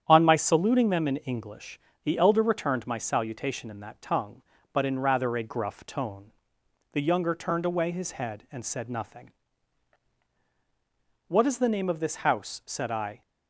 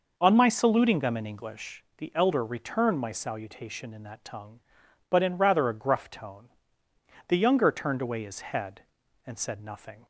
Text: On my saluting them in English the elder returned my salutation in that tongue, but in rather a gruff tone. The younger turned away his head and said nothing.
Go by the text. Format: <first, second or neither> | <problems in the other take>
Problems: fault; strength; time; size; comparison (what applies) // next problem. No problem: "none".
second | starts louder than the rest; strong; until 1.0 s; 9 dB // pauses between "English" and "the"; slight; at 1.7 s; 0.24 s long // goes on to say "What is the name of this house said I"; strong; from 11.2 s on; 1.9 s long